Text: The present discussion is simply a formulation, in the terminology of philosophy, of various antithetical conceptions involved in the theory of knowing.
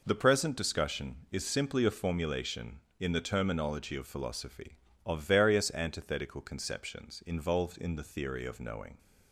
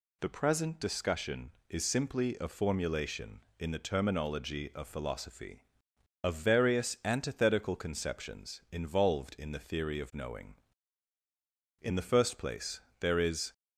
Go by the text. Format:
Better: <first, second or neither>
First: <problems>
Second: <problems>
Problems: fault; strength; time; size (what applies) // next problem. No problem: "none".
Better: first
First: none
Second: goes on to say "In the first place there is"; strong; from 11.8 s on; 1.7 s long